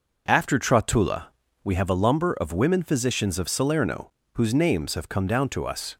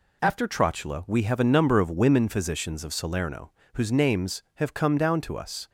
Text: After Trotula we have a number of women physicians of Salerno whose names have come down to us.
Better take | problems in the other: second | pauses between "Trotula" and "we"; slight; at 1.2 s; 0.36 s long // says "lumber" for "number"; at 1.9 s // pauses between "Salerno" and "whose"; slight; at 4.1 s; 0.22 s long; slight in the second

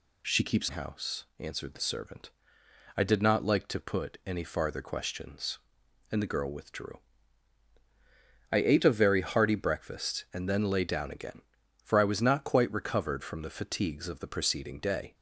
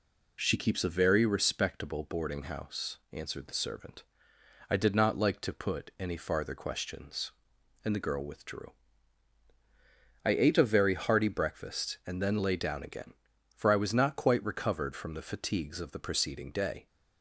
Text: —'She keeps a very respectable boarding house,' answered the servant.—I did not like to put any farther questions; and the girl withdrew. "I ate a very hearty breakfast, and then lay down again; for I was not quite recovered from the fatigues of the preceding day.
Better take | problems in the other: second | skips "a very respectable boarding"; at 0.6 s

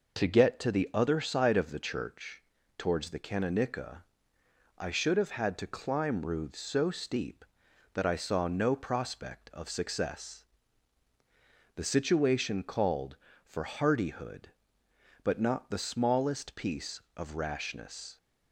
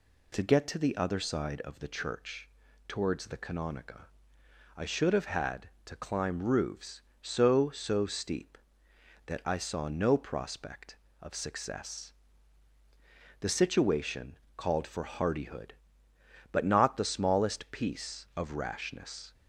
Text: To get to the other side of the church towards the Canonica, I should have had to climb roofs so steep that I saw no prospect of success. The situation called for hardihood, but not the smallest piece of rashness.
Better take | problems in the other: first | pauses between "church" and "towards"; at 2.4 s; 0.38 s long; also in the first // says "so" twice; at 7.6 s // pauses between "situation" and "called"; slight; at 14.3 s; 0.18 s long

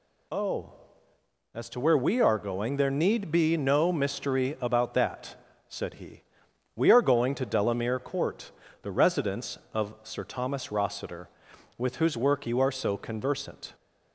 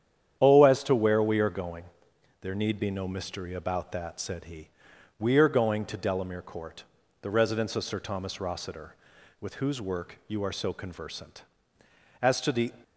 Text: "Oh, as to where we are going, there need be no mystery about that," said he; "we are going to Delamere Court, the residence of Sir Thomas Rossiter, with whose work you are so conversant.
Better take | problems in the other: first | starts louder than the rest; strong; until 1.4 s; 9.5 dB // goes on to say "As to the"; from 12.2 s on; 0.50 s long

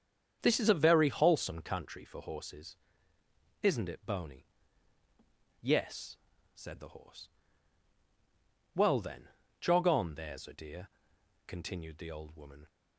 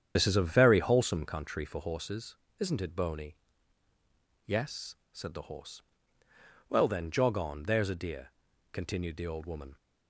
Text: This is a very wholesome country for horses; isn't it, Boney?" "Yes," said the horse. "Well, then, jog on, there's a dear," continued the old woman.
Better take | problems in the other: first | loses the start of "This"; at 0.1 s; 50 ms // starts louder than the rest; strong; until 1.1 s; 8.5 dB; strong in the first

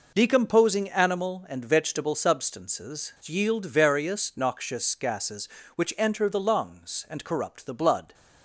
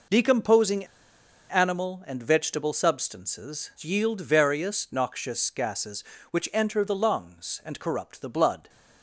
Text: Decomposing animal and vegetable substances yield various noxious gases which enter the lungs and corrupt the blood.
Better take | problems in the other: first | pauses between "Decomposing" and "animal"; noticeable; at 0.8 s; 0.63 s long

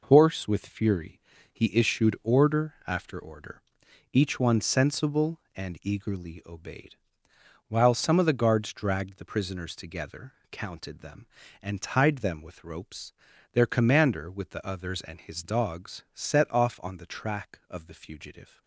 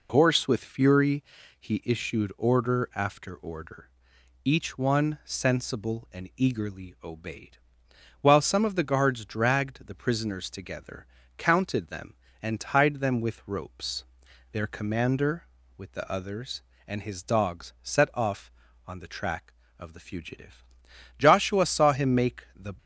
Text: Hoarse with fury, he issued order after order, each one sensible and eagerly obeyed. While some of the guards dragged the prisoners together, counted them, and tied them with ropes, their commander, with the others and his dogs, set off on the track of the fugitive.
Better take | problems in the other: first | goes on to say "Joshua saw him make the"; from 21.1 s on; 1.5 s long

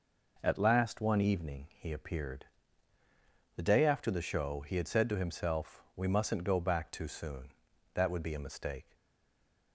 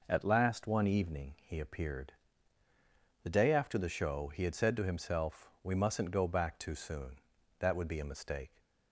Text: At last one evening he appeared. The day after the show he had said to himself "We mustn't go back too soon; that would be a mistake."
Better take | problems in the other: second | stays silent after the last word; slight; from 8.9 s on; 0.8 s long

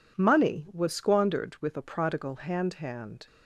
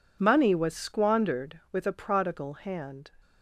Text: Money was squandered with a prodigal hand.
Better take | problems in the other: second | says "hand" twice; at 2.7 s

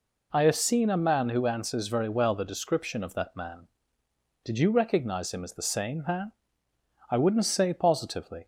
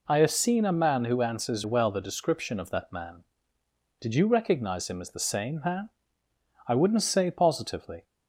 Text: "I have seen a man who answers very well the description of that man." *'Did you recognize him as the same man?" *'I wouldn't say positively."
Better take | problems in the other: first | skips "very"; at 1.6 s

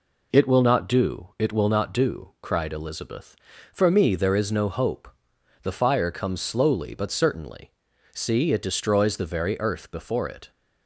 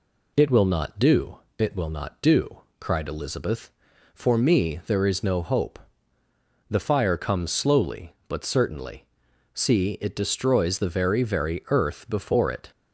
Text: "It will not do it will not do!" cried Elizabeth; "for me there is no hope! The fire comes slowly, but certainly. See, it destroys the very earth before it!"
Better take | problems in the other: first | pauses between "do" and "it"; slight; at 1.3 s; 0.18 s long // says "very" twice; at 11.2 s

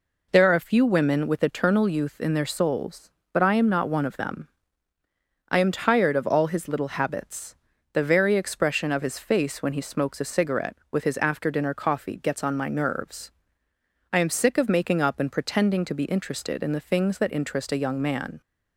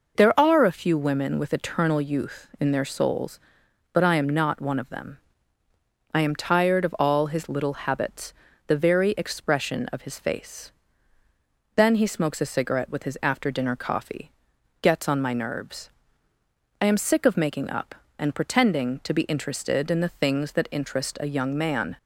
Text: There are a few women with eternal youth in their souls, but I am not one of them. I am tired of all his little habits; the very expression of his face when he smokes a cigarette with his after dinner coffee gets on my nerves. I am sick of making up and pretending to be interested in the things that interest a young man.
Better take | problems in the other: first | says "then" for "when"; at 11.7 s // pauses between "coffee" and "gets"; noticeable; at 14.3 s; 0.50 s long

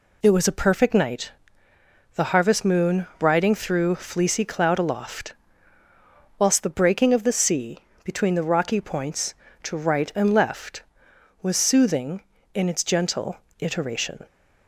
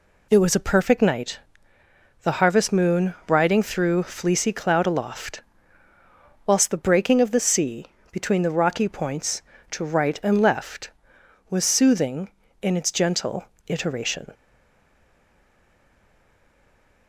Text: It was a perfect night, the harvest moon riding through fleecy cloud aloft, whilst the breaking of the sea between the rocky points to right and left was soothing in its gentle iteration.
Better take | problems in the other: first | pauses between "sea" and "between"; slight; at 7.8 s; 0.24 s long; slight in the first // pauses between "gentle" and "iteration"; slight; at 13.4 s; 0.24 s long; slight in the first // stays silent after the last word; strong; from 14.3 s on; 2.7 s long

